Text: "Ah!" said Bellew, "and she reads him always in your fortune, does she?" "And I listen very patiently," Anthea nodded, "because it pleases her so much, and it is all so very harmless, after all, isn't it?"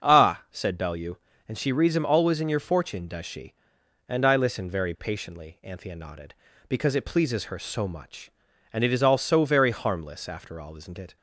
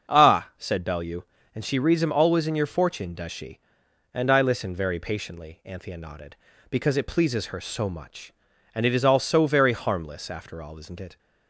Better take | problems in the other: neither | starts louder than the rest; the same in both

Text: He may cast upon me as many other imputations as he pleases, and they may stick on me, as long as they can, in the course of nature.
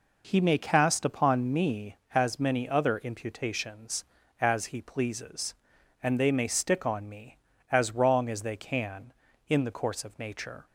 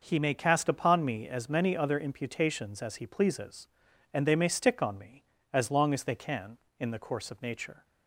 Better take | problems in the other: second | says "wrong" for "long"; at 7.9 s

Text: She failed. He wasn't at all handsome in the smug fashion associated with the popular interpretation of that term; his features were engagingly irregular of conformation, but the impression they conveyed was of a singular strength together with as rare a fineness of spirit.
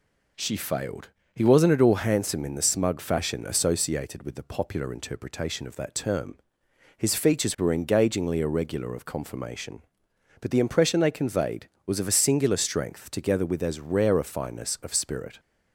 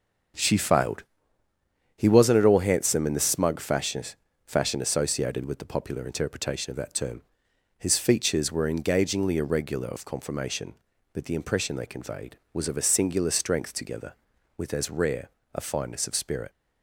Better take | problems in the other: first | starts louder than the rest; until 2.2 s; 6.5 dB // says "fashion" twice; at 4.4 s // pauses between "rare" and "a"; slight; at 15.2 s; 0.24 s long

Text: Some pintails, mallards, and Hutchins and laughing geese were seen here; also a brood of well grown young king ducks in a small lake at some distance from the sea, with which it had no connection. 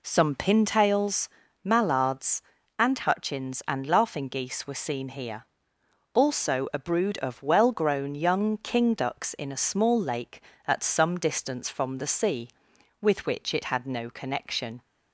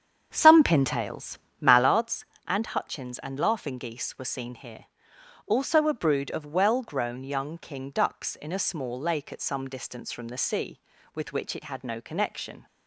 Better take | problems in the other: first | starts louder than the rest; strong; until 2.0 s; 8 dB

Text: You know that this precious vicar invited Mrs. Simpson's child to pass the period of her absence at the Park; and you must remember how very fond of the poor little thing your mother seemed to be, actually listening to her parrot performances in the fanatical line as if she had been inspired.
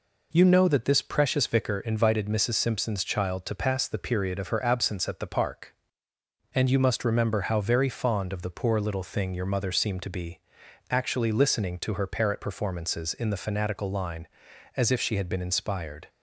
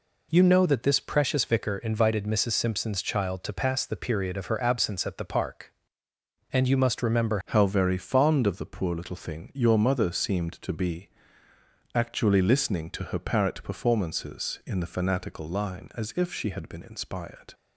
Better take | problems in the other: first | changes voice at "how"; from 7.4 s on; 10.1 s long

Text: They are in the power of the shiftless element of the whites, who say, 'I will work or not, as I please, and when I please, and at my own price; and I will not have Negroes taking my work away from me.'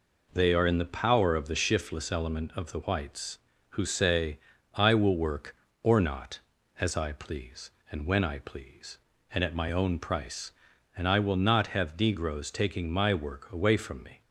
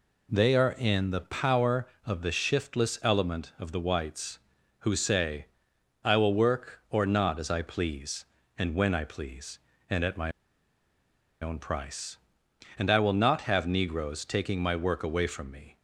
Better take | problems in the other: first | pauses between "my" and "own"; at 10.3 s; 1.1 s long

